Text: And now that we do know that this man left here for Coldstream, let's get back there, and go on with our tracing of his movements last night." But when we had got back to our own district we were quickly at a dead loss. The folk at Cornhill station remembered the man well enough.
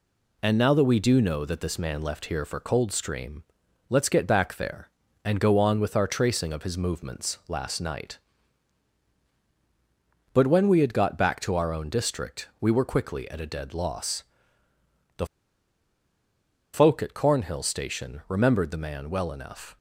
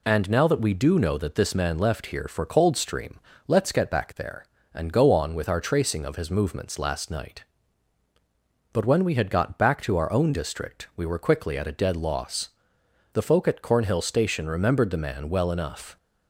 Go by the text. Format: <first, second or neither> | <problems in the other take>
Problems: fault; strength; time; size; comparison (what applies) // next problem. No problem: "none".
second | pauses between "The" and "folk"; strong; at 15.2 s; 1.4 s long